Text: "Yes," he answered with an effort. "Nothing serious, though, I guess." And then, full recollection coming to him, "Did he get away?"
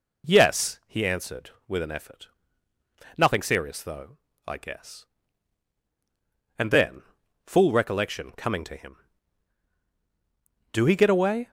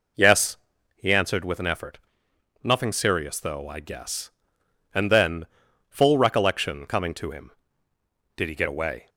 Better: second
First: says "Do" for "Did"; at 10.7 s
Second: none

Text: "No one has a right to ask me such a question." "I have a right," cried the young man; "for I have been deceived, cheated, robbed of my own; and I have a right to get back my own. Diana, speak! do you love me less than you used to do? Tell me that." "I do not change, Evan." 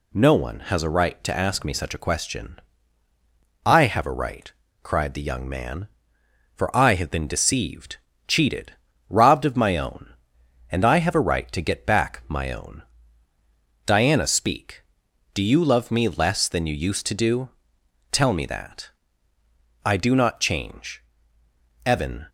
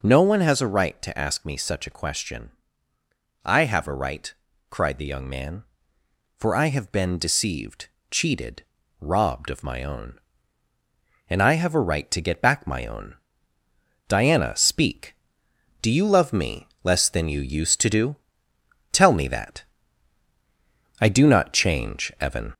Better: first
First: none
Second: gets louder; slight; throughout; 2.5 dB // pauses between "me" and "less"; slight; at 16.6 s; 0.16 s long

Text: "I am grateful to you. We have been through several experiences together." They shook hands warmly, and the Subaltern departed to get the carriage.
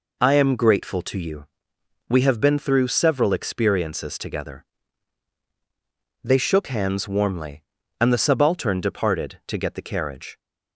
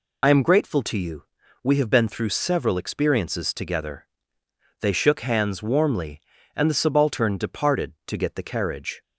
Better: first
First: none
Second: loses the start of "I"; at 0.2 s; 50 ms

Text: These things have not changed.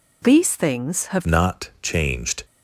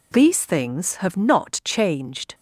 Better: second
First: changes voice at "not"; from 1.2 s on; 1.2 s long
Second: none

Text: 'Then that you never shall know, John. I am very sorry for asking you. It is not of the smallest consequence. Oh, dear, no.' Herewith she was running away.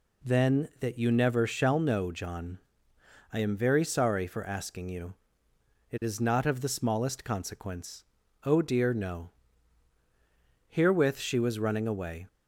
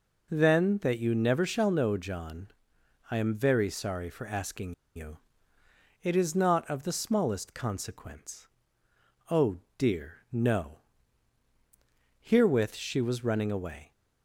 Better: first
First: none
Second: pauses between "asking" and "you"; slight; at 4.7 s; 0.23 s long

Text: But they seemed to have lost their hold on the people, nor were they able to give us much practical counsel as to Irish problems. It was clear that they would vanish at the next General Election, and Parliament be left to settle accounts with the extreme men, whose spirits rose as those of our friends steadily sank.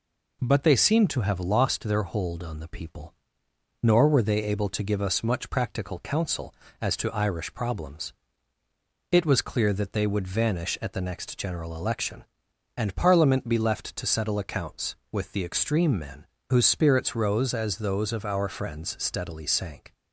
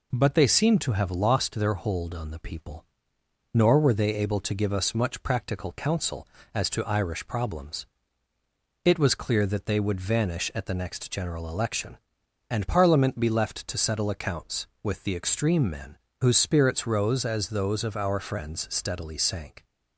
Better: neither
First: none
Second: none

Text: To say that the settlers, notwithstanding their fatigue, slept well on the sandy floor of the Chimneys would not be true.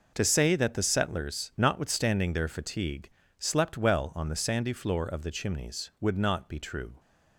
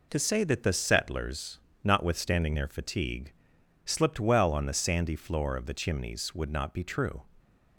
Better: first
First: none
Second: says "slipped" for "slept"; at 3.8 s

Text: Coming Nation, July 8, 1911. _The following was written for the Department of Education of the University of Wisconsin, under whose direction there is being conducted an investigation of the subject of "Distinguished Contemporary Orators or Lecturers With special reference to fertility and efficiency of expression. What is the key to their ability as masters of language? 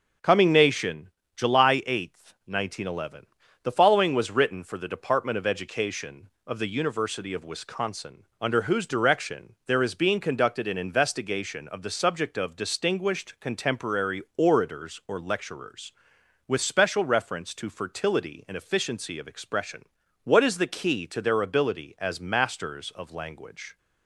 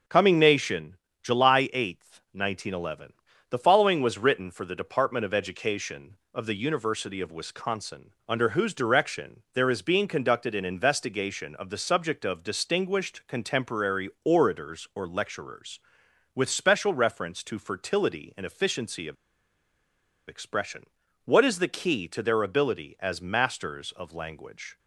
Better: first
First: starts louder than the rest; until 1.5 s; 6.5 dB // pauses between "Contemporary" and "Orators"; slight; at 14.2 s; 0.16 s long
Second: starts louder than the rest; until 1.3 s; 6.5 dB // pauses between "Contemporary" and "Orators"; slight; at 14.0 s; 0.16 s long // pauses between "of" and "expression"; at 19.1 s; 1.1 s long

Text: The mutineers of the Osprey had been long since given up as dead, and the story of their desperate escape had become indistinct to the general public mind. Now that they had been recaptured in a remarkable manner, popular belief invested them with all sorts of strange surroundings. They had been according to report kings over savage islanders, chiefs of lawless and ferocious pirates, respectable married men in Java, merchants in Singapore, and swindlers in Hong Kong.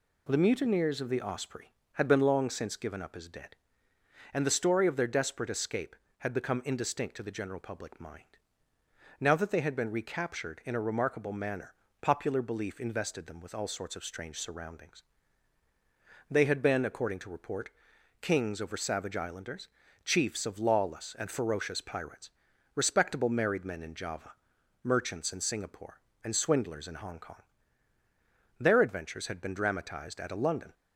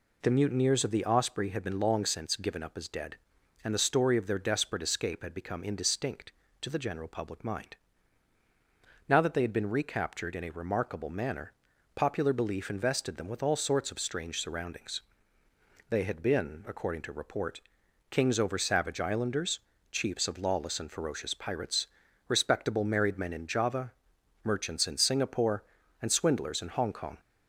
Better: second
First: pauses between "report" and "kings"; noticeable; at 17.6 s; 0.50 s long // goes on to say "Their adventures had been dramatized at a London"; strong; from 28.5 s on; 2.1 s long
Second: pauses between "report" and "kings"; noticeable; at 17.5 s; 0.52 s long

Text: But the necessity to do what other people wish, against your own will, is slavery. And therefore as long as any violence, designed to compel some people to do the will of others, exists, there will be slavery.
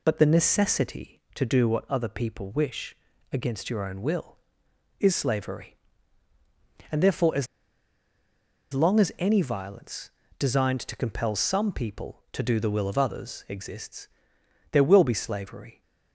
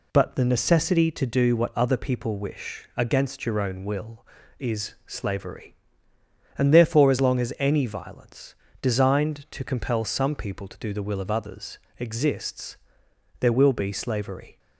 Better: second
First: pauses between "as" and "long"; strong; at 7.4 s; 1.2 s long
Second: none

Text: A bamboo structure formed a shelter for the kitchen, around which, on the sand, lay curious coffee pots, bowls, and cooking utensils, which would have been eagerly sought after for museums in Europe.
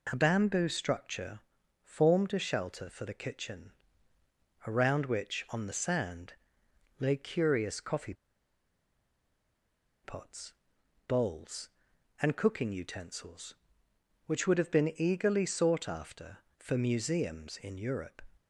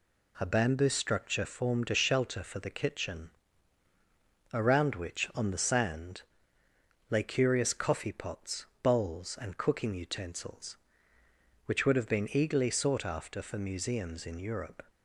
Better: second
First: pauses between "structure" and "formed"; at 1.3 s; 0.44 s long // pauses between "coffee" and "pots"; strong; at 8.1 s; 1.9 s long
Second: none

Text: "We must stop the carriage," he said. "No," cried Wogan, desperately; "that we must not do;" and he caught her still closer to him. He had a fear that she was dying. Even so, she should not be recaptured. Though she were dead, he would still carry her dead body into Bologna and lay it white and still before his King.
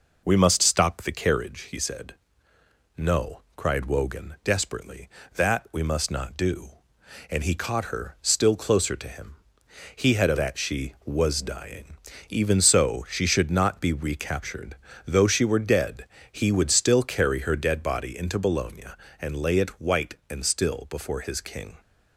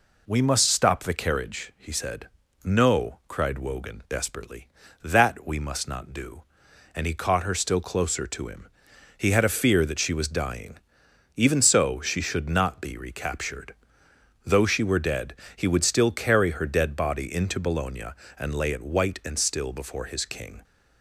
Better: second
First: skips "fear"; at 10.3 s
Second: none

